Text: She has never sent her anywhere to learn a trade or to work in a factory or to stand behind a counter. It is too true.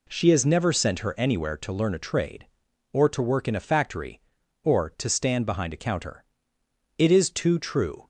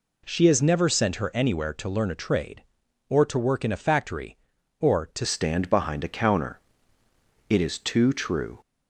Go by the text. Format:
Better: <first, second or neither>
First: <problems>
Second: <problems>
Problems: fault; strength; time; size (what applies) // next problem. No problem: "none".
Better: first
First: none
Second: changes voice at "stand"; from 5.2 s on; 3.3 s long